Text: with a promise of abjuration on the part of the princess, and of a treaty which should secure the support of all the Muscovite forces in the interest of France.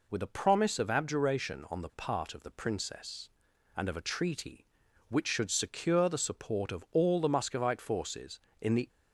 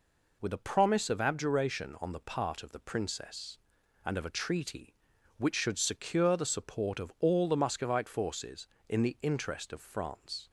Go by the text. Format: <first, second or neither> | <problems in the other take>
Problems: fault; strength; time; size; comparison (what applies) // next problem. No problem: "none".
second | stops before "interest of France"; at 8.8 s